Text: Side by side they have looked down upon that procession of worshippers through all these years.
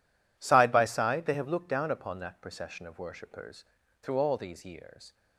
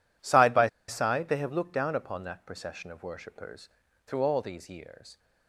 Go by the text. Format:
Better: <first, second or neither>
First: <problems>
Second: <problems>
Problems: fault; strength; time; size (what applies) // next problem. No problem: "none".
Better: first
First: pauses between "worshippers" and "through"; at 3.6 s; 0.38 s long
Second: pauses between "by" and "side"; slight; at 0.6 s; 0.20 s long // pauses between "worshippers" and "through"; at 3.6 s; 0.38 s long